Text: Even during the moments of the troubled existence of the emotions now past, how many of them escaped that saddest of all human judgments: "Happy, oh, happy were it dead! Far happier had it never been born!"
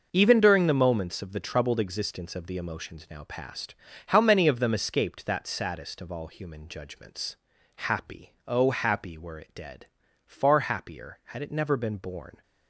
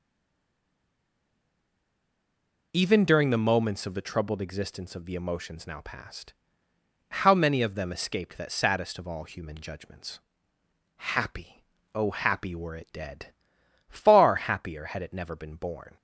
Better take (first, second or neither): first